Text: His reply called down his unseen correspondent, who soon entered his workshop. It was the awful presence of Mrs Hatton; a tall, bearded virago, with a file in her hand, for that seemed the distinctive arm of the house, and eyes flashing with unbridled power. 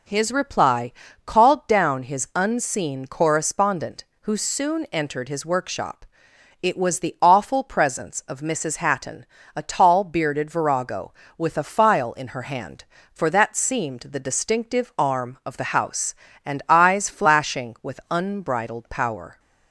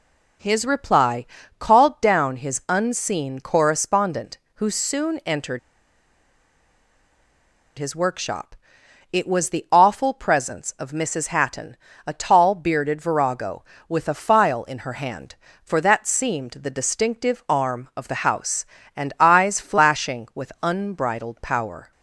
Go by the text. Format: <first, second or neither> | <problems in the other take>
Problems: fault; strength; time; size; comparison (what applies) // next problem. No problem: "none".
first | pauses between "reply" and "called"; slight; at 1.2 s; 0.32 s long; slight in the first // pauses between "entered" and "his"; strong; at 5.5 s; 2.1 s long